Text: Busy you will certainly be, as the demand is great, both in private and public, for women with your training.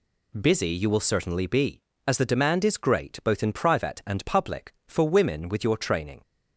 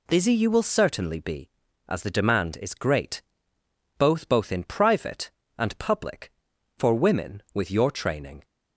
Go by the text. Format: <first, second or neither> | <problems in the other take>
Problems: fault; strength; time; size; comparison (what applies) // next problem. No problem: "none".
first | says "both" twice; at 4.2 s